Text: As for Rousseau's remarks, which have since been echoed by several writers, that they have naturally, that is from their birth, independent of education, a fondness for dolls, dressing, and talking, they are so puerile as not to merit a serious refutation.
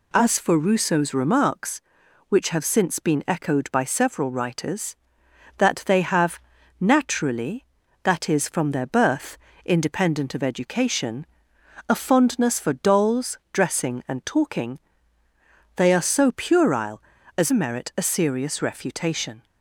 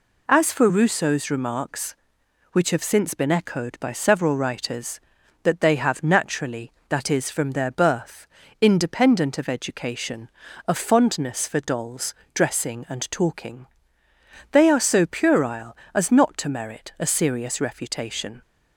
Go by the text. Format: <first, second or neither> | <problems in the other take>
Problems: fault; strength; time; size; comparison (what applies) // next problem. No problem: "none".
second | pauses between "have" and "naturally"; at 6.3 s; 0.44 s long // skips "not to"; at 17.5 s